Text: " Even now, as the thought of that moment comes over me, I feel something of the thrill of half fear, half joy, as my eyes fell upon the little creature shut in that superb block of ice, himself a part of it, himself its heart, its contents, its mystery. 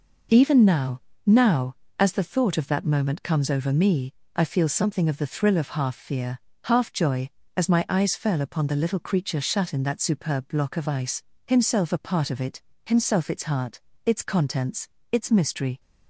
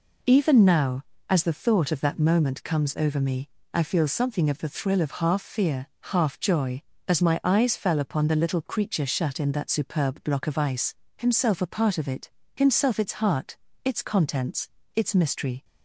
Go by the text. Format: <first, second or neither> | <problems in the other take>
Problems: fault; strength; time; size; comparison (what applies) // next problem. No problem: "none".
second | says "now" twice; at 1.2 s